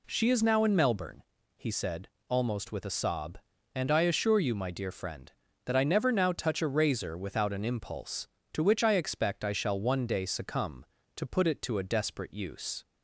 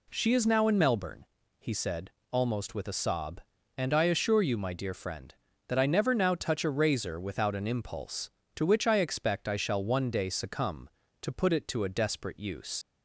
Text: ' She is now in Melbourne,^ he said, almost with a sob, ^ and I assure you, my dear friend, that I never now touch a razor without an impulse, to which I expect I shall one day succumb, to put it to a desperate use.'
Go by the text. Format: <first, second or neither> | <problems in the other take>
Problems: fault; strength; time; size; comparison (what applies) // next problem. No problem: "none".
first | leaves "use" unfinished; at 12.8 s; 80 ms